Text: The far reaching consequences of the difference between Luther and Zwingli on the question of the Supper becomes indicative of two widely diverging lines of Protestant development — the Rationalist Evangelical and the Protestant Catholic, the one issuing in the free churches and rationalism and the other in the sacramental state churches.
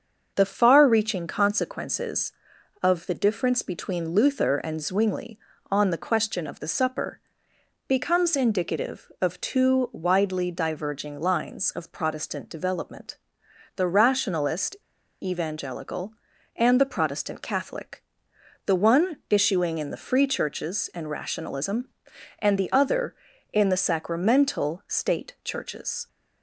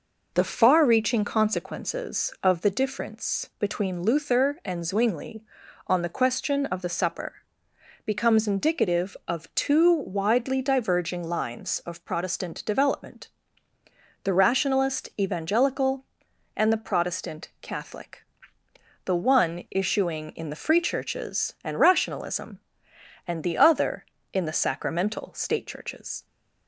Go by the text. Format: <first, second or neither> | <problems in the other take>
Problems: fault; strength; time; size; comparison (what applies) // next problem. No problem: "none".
second | starts louder than the rest; until 1.3 s; 7 dB // pauses between "Supper" and "becomes"; noticeable; at 7.1 s; 0.68 s long; noticeable in the second // pauses between "Rationalist" and "Evangelical"; noticeable; at 14.7 s; 0.45 s long